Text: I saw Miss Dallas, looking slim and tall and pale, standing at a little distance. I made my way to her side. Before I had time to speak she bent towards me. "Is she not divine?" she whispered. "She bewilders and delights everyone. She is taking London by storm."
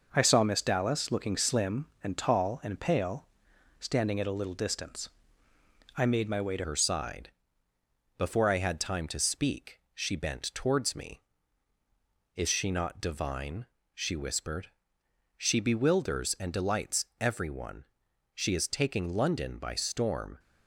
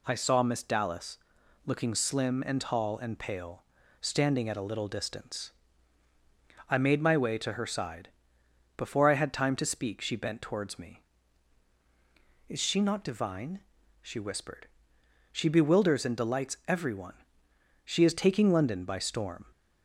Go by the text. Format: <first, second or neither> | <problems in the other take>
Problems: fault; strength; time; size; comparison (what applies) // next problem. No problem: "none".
second | changes voice at "her"; from 6.6 s on; 13.7 s long // pauses between "speak" and "she"; slight; at 9.7 s; 0.16 s long // pauses between "delights" and "everyone"; slight; at 17.0 s; 0.16 s long